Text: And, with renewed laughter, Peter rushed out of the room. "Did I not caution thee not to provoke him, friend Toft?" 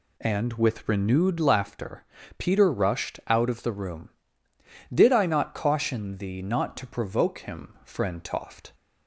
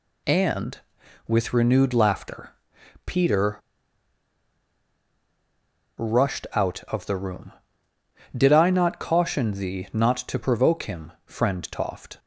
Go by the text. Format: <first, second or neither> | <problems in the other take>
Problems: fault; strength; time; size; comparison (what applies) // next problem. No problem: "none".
first | pauses between "Peter" and "rushed"; strong; at 3.5 s; 2.3 s long